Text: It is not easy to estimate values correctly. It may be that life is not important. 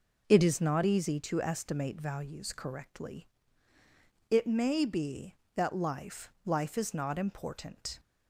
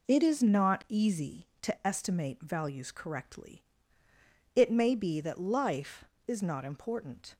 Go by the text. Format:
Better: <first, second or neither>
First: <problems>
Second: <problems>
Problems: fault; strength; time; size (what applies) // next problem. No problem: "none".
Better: second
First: says "life" twice; at 6.4 s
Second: none